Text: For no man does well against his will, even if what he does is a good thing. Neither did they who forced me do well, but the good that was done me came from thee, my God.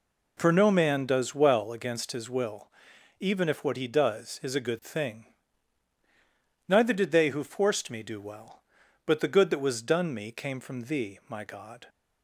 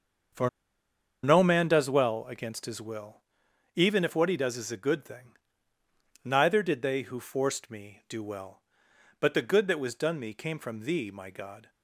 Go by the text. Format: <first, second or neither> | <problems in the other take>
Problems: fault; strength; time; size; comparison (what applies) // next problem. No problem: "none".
first | starts louder than the rest; until 2.0 s; 7 dB // pauses between "For" and "no"; noticeable; at 0.4 s; 0.74 s long